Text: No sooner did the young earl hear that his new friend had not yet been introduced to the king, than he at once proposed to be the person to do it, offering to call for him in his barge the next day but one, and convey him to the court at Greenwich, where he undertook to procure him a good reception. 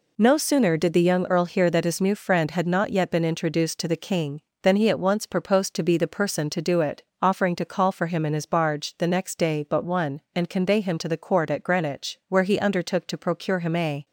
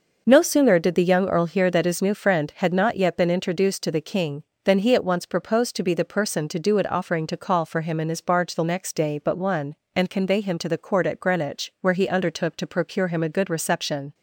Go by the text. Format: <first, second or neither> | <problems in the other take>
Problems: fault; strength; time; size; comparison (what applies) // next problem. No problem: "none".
second | stops before "good reception"; at 14.0 s